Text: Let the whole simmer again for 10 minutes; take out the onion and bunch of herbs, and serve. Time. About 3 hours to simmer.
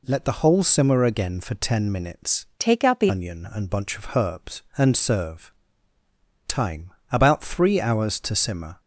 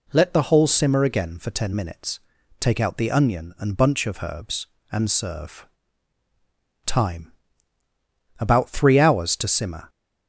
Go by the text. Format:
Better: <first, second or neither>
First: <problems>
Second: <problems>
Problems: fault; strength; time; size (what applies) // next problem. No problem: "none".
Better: second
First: changes voice from "take" to "the"; from 2.5 to 3.1 s; 0.6 s long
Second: none